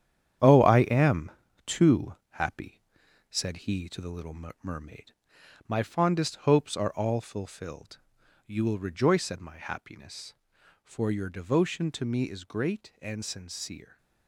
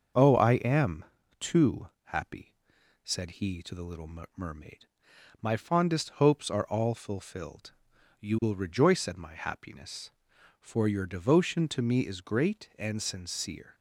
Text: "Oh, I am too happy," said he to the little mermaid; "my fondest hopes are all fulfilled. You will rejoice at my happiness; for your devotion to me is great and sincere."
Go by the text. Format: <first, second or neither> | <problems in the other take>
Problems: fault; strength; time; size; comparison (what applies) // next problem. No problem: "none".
second | gets quieter; strong; throughout; 9 dB // starts louder than the rest; strong; until 1.7 s; 9.5 dB; also in the second // pauses between "am" and "too"; slight; at 1.2 s; 0.36 s long; slight in the second // pauses between "little" and "mermaid"; slight; at 4.3 s; 0.28 s long; slight in the second